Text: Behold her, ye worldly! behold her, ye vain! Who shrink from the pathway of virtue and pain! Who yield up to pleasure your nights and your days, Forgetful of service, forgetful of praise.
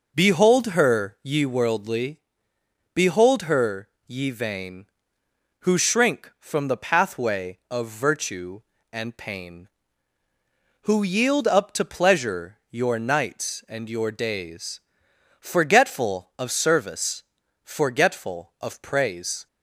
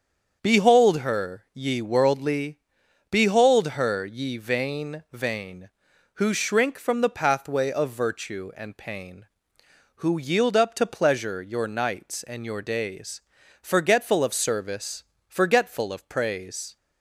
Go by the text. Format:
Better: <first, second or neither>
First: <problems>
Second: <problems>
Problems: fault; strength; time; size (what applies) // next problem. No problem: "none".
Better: first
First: none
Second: starts louder than the rest; strong; until 1.4 s; 7.5 dB // says "vain" twice; at 5.1 s